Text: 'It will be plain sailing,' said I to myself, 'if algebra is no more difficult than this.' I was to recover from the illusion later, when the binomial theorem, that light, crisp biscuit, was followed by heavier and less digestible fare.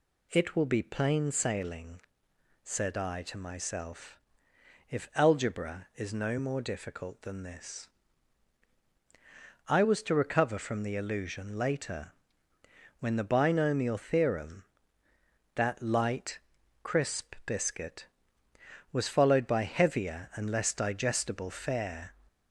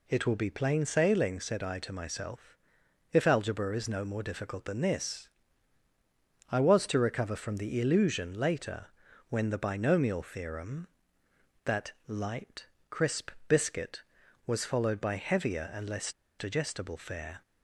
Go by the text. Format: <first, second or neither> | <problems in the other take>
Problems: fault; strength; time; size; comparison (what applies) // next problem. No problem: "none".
first | pauses between "crisp" and "biscuit"; slight; at 13.2 s; 0.18 s long // pauses between "less" and "digestible"; slight; at 16.1 s; 0.26 s long